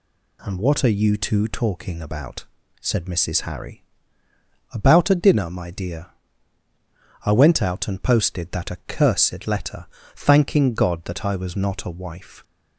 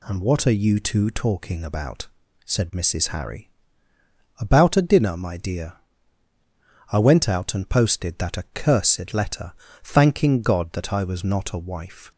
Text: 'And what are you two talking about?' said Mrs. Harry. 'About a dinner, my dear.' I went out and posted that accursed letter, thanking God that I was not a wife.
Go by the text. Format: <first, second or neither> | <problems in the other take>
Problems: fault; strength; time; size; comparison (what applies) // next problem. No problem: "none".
neither | none